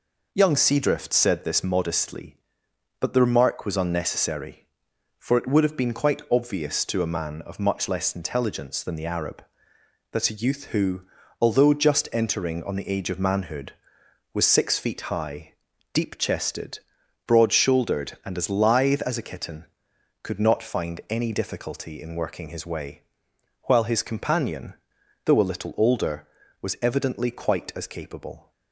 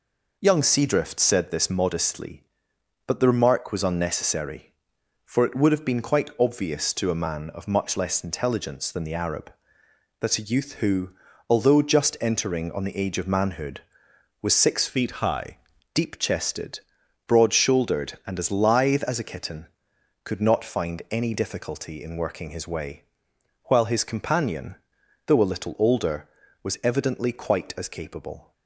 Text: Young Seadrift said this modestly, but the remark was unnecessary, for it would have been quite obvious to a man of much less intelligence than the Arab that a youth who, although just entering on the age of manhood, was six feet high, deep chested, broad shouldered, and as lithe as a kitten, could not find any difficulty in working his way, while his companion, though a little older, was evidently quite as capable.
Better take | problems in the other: first | changes voice from "feet" to "high"; from 14.8 to 15.5 s; 0.7 s long

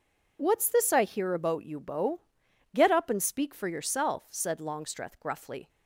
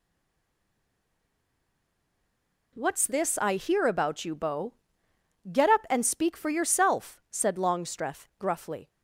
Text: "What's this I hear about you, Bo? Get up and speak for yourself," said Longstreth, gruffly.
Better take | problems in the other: first | stays silent before the first word; strong; until 2.7 s; 2.7 s long

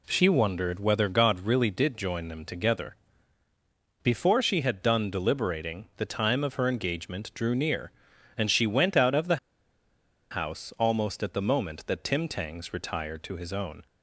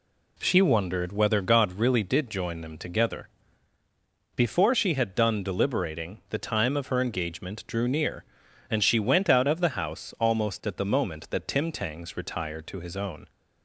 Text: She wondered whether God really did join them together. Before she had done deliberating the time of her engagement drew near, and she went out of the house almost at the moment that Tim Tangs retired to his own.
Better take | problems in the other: second | pauses between "the" and "house"; noticeable; at 9.3 s; 0.93 s long

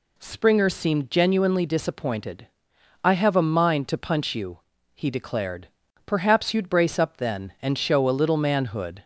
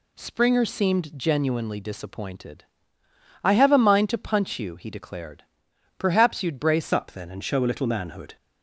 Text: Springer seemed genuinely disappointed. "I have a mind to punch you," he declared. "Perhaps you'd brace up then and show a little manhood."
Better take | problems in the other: first | changes voice at "up"; from 6.9 s on; 1.4 s long

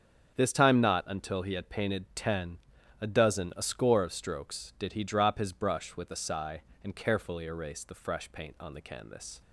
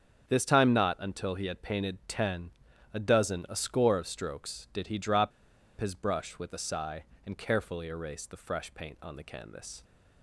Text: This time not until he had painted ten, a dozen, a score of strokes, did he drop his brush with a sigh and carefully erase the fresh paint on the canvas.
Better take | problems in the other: first | starts louder than the rest; strong; until 1.3 s; 8 dB; strong in the first // pauses between "drop" and "his"; noticeable; at 5.3 s; 0.50 s long

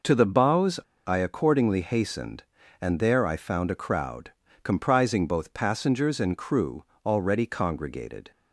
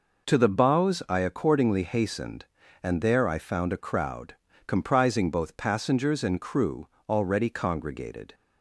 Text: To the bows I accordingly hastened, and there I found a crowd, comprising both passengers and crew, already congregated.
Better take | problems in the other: second | pauses between "bows" and "I"; slight; at 0.7 s; 0.26 s long

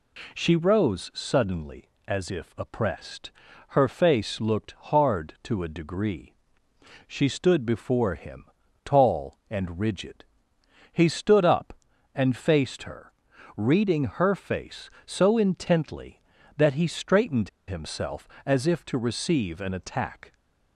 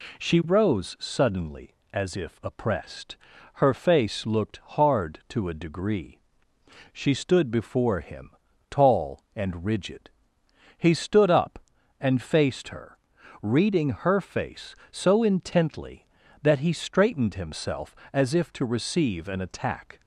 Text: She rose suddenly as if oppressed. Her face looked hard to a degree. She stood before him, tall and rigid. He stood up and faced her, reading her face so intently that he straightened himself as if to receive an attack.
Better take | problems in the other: second | pauses between "straightened" and "himself"; slight; at 17.4 s; 0.18 s long

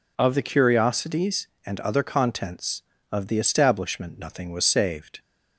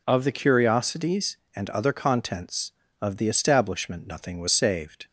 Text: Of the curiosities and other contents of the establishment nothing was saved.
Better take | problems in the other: neither | none

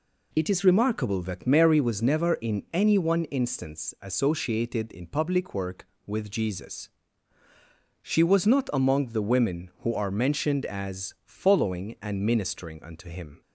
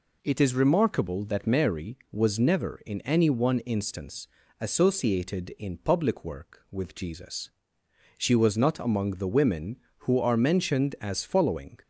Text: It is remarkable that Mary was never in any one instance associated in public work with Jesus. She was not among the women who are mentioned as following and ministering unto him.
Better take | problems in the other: first | pauses between "instance" and "associated"; slight; at 4.2 s; 0.32 s long // stops before "and ministering unto him"; at 11.8 s

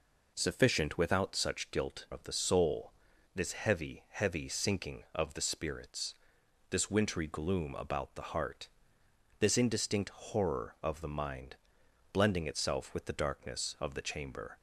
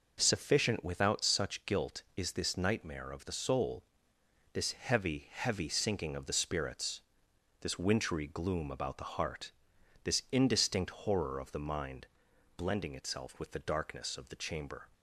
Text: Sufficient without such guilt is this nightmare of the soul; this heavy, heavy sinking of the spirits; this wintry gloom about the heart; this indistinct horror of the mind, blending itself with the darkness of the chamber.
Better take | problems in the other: second | skips "is this nightmare"; at 2.0 s

